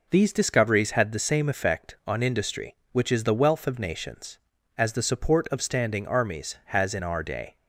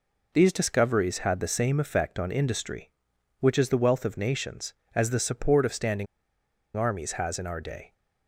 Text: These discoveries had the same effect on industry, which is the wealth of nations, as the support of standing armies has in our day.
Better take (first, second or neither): first